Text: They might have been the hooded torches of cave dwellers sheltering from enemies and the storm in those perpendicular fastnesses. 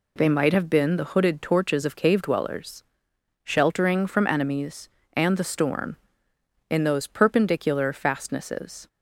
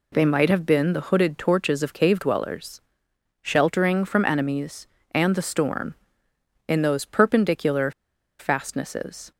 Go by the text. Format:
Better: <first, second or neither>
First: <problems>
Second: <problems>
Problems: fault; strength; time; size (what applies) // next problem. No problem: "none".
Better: first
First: pauses between "dwellers" and "sheltering"; noticeable; at 2.8 s; 0.59 s long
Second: pauses between "dwellers" and "sheltering"; noticeable; at 2.8 s; 0.60 s long // pauses between "perpendicular" and "fastnesses"; noticeable; at 7.9 s; 0.47 s long